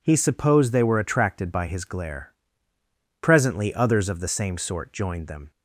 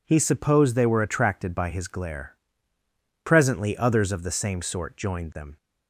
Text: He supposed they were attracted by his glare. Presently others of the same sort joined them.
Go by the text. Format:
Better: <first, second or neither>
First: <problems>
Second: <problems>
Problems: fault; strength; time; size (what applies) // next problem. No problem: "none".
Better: neither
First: none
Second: none